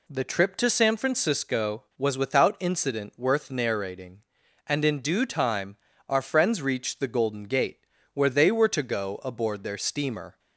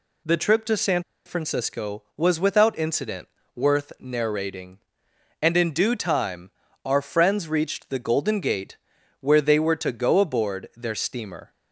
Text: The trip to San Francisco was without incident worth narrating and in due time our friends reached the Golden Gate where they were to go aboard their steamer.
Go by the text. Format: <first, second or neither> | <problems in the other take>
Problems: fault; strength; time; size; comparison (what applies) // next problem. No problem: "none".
first | pauses between "San" and "Francisco"; slight; at 1.0 s; 0.24 s long // pauses between "incident" and "worth"; slight; at 3.2 s; 0.30 s long // pauses between "time" and "our"; slight; at 6.4 s; 0.34 s long; slight in the first // pauses between "Gate" and "where"; at 8.7 s; 0.44 s long; slight in the first